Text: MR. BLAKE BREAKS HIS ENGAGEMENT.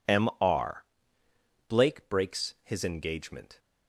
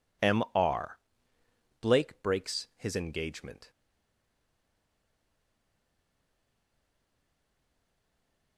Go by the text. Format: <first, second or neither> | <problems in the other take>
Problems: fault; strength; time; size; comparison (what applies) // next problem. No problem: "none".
first | stays silent after the last word; strong; from 3.7 s on; 4.8 s long